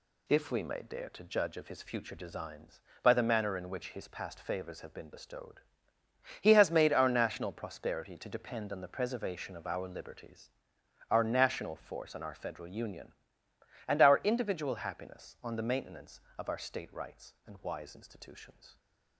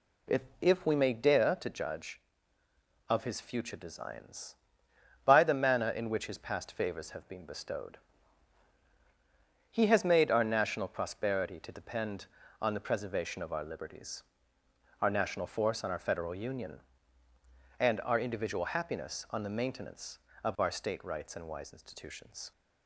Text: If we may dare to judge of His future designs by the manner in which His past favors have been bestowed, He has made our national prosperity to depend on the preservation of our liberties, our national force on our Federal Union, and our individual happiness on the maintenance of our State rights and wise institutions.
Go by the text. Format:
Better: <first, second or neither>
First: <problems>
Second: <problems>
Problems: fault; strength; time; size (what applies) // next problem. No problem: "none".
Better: first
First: none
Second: says "If" twice; at 0.6 s